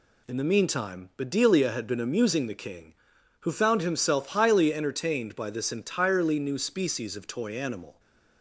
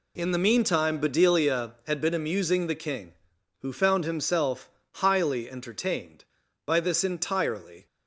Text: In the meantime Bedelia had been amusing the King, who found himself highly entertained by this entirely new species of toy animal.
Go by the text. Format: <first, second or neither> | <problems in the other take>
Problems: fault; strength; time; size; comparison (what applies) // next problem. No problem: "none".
first | pauses between "himself" and "highly"; slight; at 4.7 s; 0.24 s long // stops before "new species of toy animal"; at 7.8 s